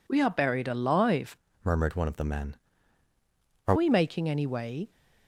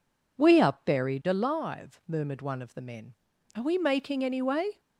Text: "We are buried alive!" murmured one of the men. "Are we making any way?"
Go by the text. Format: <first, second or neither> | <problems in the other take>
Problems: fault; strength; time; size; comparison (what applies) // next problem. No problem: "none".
second | changes voice from "murmured" to "Are"; from 1.6 to 3.7 s; 2.1 s long